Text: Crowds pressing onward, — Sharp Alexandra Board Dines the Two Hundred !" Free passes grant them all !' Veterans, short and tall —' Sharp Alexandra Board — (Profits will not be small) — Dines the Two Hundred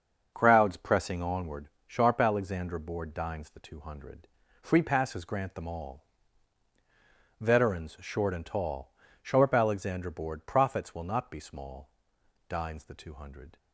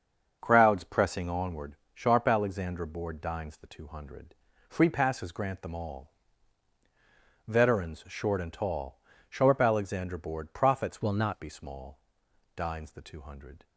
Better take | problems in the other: first | starts louder than the rest; until 1.4 s; 6.5 dB; also in the first // changes voice from "will" to "not"; from 11.0 to 11.3 s; 0.3 s long

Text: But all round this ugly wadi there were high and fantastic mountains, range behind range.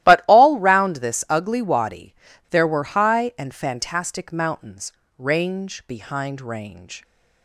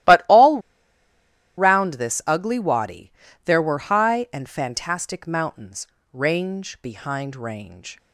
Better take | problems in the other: first | starts louder than the rest; strong; until 2.0 s; 14.5 dB; strong in the first // pauses between "all" and "round"; at 0.5 s; 0.98 s long // pauses between "wadi" and "there"; slight; at 3.1 s; 0.34 s long; also in the first

